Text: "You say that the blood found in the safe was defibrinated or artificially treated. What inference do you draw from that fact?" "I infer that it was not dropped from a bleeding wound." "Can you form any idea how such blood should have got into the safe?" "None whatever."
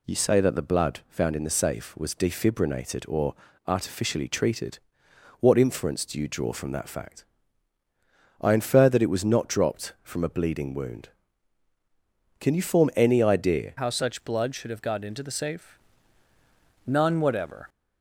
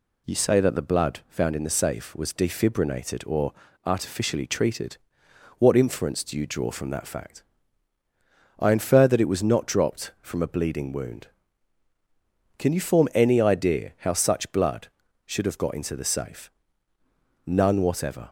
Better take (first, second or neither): second